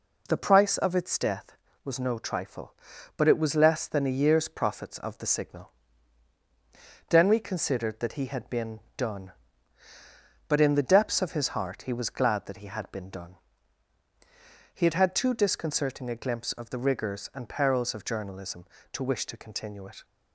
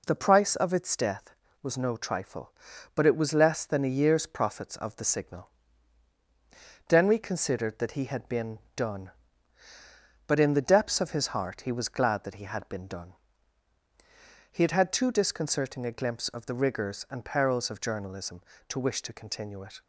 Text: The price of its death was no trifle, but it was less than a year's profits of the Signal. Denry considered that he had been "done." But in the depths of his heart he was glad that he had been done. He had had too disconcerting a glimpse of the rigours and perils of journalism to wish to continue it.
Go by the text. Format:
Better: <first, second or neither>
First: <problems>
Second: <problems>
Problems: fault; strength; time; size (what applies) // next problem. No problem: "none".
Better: neither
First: pauses between "been" and "done"; slight; at 8.7 s; 0.16 s long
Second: pauses between "been" and "done"; slight; at 8.5 s; 0.16 s long